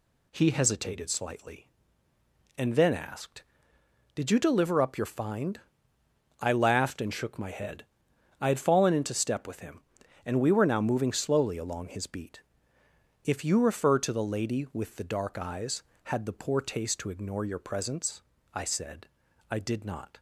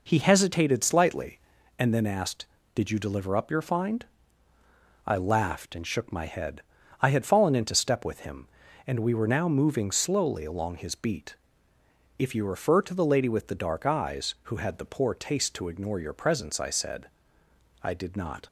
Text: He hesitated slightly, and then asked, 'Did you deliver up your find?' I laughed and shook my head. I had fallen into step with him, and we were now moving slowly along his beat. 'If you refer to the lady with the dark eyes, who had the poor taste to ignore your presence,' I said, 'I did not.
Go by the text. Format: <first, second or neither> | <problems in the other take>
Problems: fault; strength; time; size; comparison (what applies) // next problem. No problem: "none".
second | skips "who"; at 15.9 s